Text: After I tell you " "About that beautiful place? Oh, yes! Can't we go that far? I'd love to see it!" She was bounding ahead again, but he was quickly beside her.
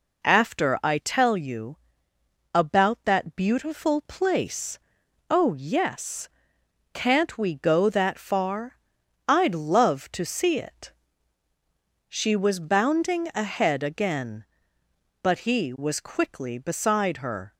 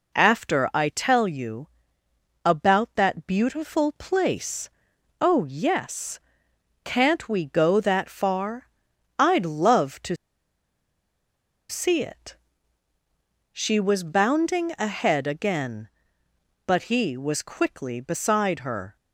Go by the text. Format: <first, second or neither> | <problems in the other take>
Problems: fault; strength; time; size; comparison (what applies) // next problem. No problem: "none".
first | pauses between "to" and "see"; strong; at 10.1 s; 1.5 s long